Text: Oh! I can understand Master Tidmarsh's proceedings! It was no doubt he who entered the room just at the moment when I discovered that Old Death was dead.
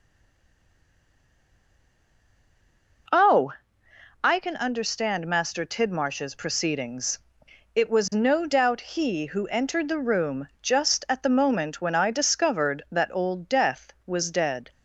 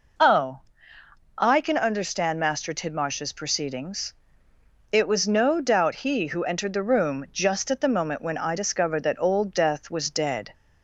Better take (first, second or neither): second